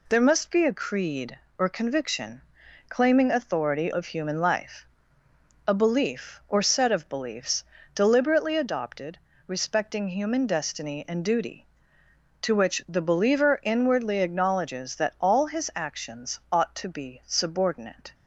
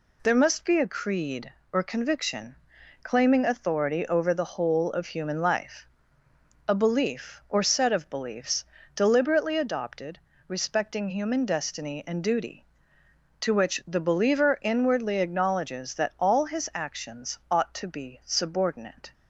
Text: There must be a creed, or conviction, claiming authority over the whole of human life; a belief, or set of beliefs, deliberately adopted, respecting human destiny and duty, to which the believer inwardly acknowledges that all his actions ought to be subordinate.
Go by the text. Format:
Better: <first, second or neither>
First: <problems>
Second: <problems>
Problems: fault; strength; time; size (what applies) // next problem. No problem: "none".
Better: second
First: skips "over the whole"; at 3.9 s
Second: none